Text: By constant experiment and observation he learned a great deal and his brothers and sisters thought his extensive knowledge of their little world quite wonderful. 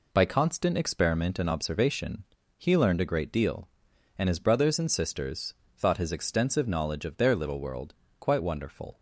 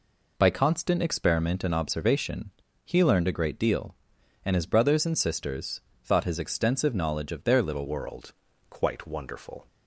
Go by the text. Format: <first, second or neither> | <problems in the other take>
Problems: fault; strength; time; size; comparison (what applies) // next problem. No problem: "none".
first | pauses between "observation" and "he"; slight; at 2.5 s; 0.34 s long; slight in the first // pauses between "sisters" and "thought"; slight; at 5.8 s; 0.24 s long; slight in the first // changes voice at "world"; from 7.8 s on; 1.8 s long // pauses between "world" and "quite"; slight; at 8.3 s; 0.36 s long; slight in the first